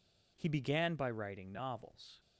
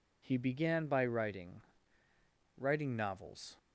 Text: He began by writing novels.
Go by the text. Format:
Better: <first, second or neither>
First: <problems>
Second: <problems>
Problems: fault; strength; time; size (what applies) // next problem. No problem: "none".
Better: first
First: none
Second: says "writing" twice; at 2.5 s